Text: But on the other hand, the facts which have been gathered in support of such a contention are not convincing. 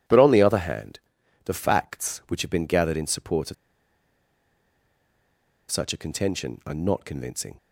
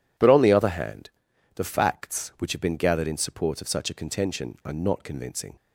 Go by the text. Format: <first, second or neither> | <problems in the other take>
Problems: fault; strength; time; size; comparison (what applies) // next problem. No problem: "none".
second | pauses between "of" and "such"; strong; at 3.5 s; 2.1 s long